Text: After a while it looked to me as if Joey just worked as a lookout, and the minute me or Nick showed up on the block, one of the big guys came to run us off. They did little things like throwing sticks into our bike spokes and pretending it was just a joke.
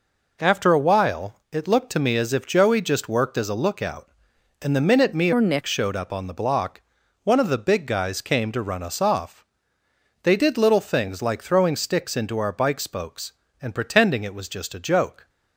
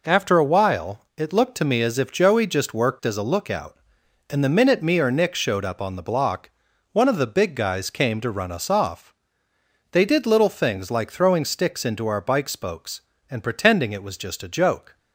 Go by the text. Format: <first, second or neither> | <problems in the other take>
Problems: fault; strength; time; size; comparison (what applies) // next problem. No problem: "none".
second | pauses between "while" and "it"; slight; at 1.3 s; 0.18 s long; slight in the second // changes voice from "or" to "Nick"; from 5.3 to 5.6 s; 0.3 s long